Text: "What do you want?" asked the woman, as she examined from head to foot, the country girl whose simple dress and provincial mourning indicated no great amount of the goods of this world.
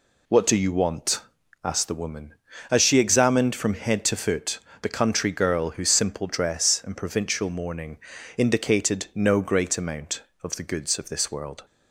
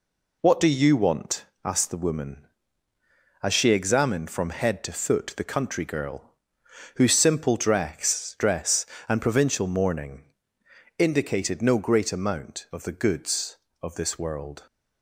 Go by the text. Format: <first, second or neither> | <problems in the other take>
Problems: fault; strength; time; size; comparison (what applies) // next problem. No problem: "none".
first | pauses between "girl" and "whose"; noticeable; at 6.3 s; 0.60 s long // says "dress" twice; at 8.3 s // pauses between "mourning" and "indicated"; noticeable; at 10.2 s; 0.74 s long; slight in the first